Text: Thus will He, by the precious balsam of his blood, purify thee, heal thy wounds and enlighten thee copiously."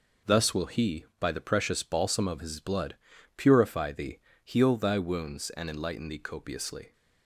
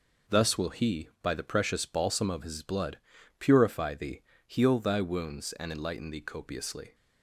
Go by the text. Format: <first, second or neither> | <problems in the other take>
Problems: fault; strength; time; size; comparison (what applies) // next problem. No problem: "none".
neither | none